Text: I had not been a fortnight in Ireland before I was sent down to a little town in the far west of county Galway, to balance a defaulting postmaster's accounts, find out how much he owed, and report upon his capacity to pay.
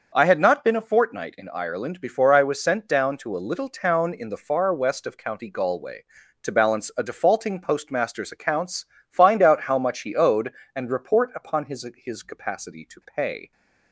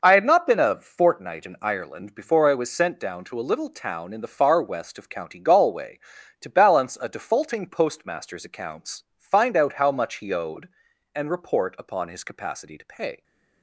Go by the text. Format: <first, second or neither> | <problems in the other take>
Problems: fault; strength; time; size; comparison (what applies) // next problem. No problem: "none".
second | starts louder than the rest; until 1.1 s; 6 dB // says "his" twice; at 11.9 s